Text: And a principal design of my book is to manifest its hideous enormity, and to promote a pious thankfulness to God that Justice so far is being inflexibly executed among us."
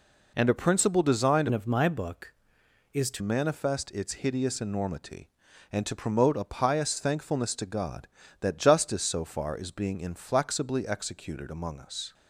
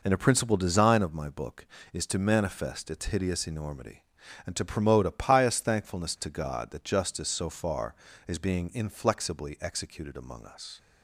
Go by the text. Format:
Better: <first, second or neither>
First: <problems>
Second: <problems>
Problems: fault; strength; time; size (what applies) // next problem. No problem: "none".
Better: second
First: changes voice from "of" to "to"; from 1.5 to 3.2 s; 1.7 s long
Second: none